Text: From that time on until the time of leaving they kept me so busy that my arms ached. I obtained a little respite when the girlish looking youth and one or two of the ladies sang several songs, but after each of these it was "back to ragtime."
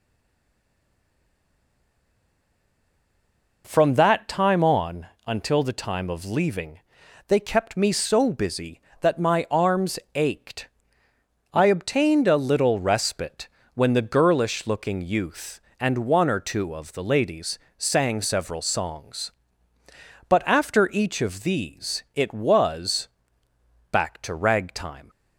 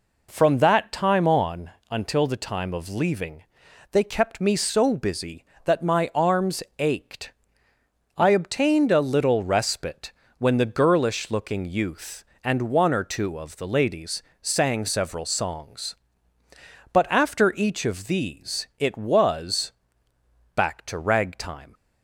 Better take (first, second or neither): second